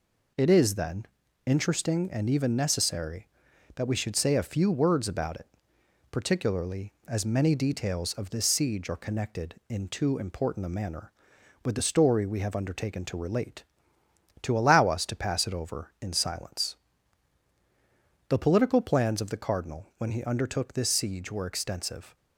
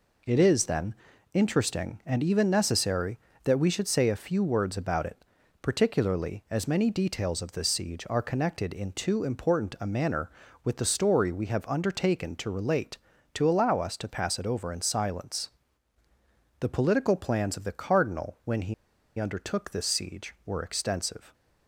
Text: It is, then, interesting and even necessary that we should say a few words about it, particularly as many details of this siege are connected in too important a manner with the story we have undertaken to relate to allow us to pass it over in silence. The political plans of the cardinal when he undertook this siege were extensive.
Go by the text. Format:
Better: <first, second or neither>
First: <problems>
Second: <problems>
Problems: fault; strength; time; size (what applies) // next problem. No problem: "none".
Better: first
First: none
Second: pauses between "he" and "undertook"; at 18.7 s; 0.44 s long